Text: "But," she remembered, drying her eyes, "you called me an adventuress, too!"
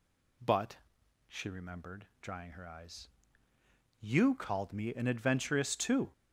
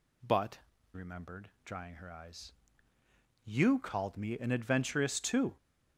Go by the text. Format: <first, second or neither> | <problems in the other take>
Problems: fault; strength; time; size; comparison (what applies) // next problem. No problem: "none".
first | skips "she"; at 0.7 s